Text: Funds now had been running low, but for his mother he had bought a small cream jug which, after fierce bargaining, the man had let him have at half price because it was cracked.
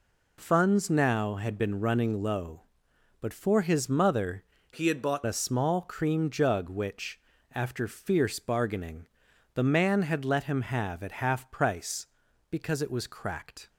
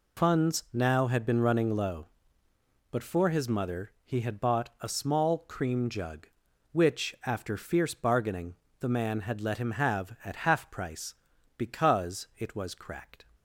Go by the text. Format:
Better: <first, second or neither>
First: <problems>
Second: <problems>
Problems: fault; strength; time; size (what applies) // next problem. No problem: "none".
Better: second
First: changes voice from "he" to "bought"; from 4.7 to 5.2 s; 0.5 s long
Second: none